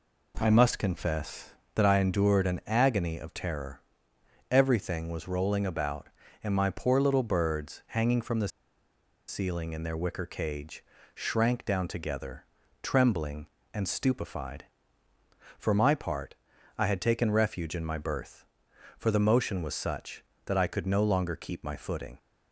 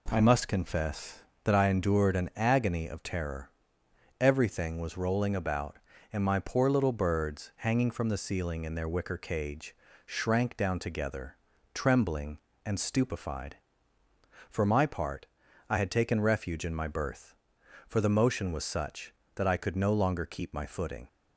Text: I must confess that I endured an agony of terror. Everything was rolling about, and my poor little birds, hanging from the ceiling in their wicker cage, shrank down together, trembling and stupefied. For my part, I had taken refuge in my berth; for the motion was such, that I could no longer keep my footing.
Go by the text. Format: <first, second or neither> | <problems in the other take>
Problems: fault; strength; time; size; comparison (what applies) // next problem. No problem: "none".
second | pauses between "the" and "ceiling"; noticeable; at 8.4 s; 0.80 s long